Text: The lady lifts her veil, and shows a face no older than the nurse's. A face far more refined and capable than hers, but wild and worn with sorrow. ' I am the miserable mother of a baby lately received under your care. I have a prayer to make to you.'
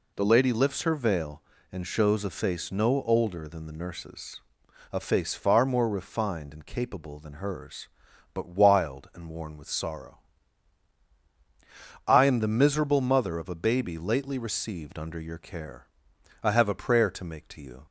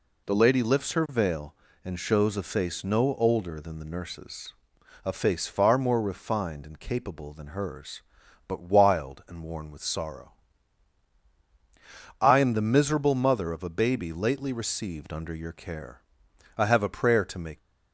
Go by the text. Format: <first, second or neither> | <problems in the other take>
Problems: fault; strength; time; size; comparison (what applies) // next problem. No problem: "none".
first | stops before "to you"; at 17.5 s